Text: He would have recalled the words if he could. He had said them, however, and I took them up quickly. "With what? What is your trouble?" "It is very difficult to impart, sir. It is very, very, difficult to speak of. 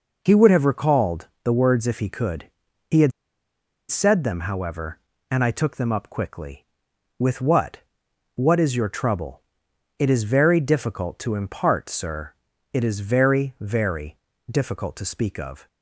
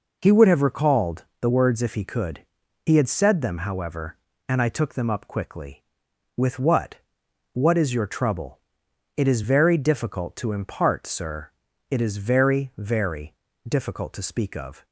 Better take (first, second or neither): second